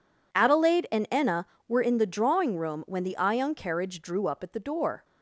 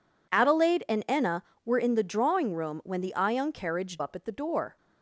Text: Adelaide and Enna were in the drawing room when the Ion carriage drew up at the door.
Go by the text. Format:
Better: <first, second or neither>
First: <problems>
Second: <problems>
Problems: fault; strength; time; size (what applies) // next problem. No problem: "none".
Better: first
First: none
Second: skips "drew"; at 3.9 s